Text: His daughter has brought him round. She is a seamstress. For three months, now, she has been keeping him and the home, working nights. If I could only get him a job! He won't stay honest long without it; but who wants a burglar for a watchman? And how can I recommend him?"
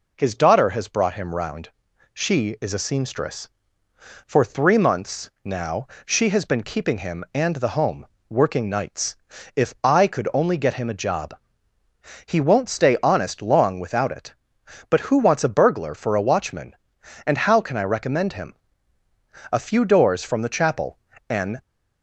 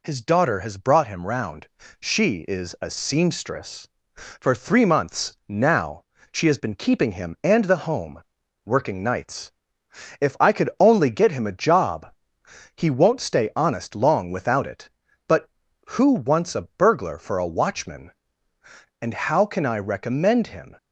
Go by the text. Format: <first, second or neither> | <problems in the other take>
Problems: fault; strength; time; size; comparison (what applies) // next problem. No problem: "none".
second | goes on to say "A few doors from the chapel an"; strong; from 19.5 s on; 2.1 s long